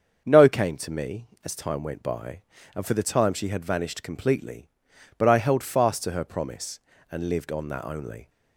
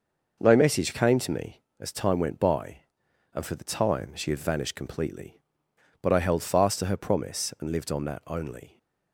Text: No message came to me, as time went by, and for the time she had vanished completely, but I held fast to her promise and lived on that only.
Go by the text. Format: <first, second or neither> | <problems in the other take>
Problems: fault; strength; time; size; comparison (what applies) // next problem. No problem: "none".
second | starts louder than the rest; until 1.2 s; 7 dB // skips "message"; at 0.4 s